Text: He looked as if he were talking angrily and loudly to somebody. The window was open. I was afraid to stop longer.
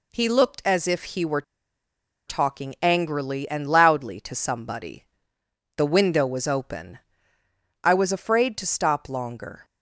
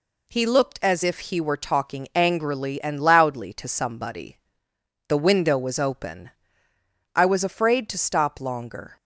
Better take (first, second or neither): second